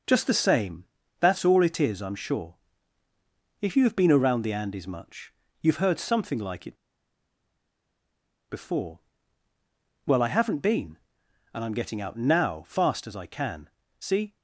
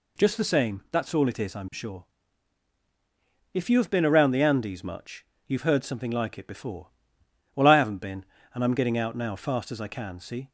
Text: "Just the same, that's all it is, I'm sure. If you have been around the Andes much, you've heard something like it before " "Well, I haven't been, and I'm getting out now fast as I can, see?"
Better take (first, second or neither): second